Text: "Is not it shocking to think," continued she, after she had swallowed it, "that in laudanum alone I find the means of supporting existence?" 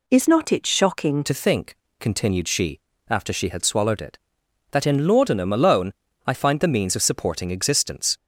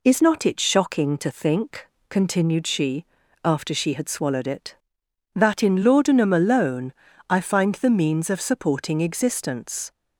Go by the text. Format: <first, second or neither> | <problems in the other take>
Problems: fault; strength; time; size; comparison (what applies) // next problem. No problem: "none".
second | changes voice at "to"; from 1.2 s on; 6.9 s long // pauses between "alone" and "I"; slight; at 5.9 s; 0.34 s long; slight in the second